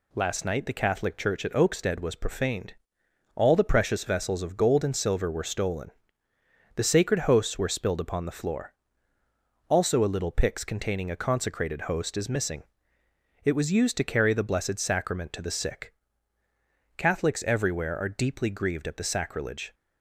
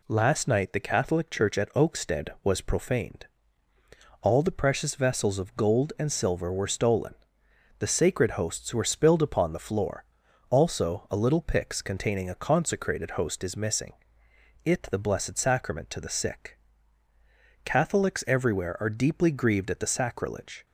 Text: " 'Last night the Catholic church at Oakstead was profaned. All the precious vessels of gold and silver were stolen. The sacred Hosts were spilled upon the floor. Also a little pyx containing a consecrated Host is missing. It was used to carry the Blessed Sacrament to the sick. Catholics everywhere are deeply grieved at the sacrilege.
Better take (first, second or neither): first